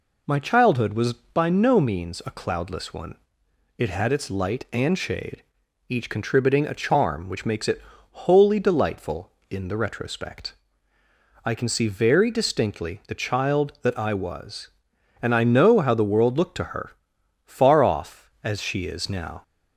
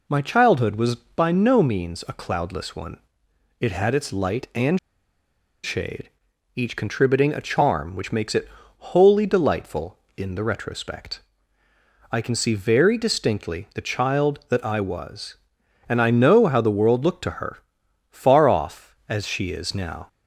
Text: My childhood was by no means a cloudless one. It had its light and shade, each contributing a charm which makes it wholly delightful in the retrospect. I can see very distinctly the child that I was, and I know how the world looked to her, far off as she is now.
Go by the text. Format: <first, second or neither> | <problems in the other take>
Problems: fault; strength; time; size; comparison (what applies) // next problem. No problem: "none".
first | pauses between "and" and "shade"; noticeable; at 4.7 s; 0.84 s long // pauses between "it" and "wholly"; slight; at 8.4 s; 0.30 s long; slight in the first